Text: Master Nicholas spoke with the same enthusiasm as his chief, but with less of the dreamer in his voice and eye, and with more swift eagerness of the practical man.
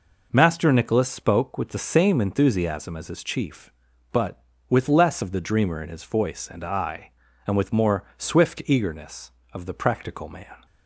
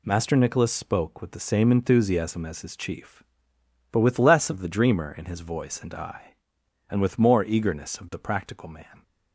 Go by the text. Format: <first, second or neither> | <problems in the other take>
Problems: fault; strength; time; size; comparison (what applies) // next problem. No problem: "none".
first | skips "swift"; at 7.4 s